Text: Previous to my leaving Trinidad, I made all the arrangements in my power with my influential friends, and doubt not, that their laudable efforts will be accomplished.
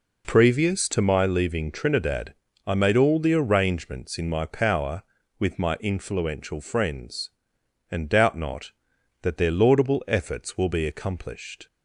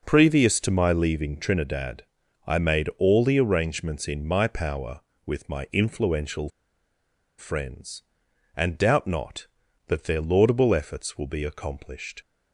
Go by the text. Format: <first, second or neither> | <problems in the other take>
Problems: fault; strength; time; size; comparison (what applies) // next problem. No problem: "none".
first | pauses between "influential" and "friends"; noticeable; at 6.4 s; 0.88 s long